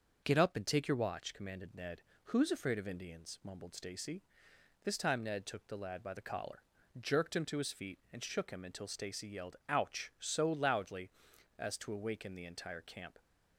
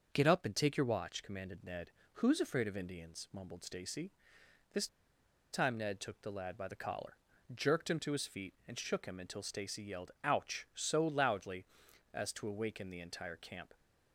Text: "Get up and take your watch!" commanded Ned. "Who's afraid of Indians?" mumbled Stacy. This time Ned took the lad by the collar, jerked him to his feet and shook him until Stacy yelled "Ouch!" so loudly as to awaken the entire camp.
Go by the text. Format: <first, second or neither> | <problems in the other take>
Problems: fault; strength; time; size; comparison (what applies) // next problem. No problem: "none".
first | starts louder than the rest; until 1.1 s; 6.5 dB; also in the first // pauses between "This" and "time"; noticeable; at 4.8 s; 0.65 s long